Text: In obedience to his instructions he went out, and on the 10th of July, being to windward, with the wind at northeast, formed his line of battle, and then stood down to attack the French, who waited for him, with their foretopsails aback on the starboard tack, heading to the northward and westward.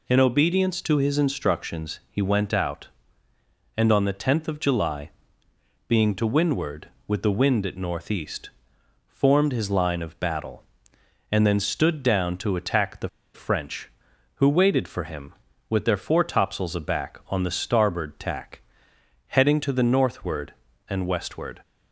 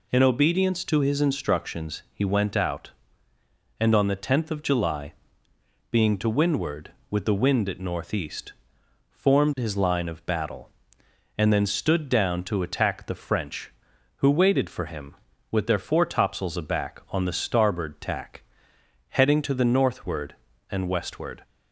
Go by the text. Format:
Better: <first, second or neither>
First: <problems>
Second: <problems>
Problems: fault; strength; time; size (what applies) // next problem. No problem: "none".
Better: second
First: pauses between "the" and "French"; slight; at 13.0 s; 0.26 s long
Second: none